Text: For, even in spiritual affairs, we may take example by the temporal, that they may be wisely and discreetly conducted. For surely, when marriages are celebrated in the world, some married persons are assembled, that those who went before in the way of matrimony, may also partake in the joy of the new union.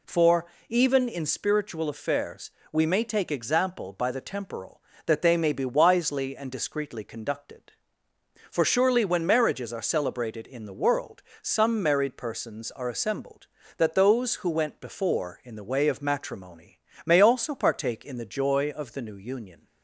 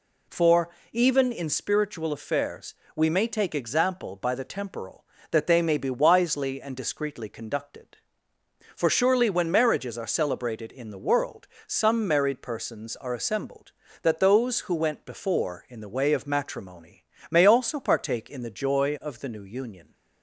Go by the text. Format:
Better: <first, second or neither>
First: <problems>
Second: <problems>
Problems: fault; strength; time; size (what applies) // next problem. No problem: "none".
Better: neither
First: none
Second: none